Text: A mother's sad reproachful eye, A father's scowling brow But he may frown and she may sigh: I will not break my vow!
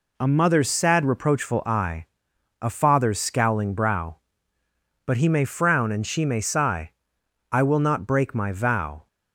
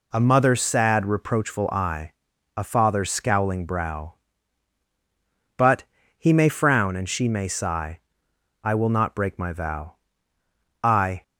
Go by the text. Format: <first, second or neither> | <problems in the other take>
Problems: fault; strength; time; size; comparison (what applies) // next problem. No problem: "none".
first | pauses between "But" and "he"; slight; at 5.8 s; 0.34 s long // goes on to say "I"; slight; from 10.8 s on; 0.40 s long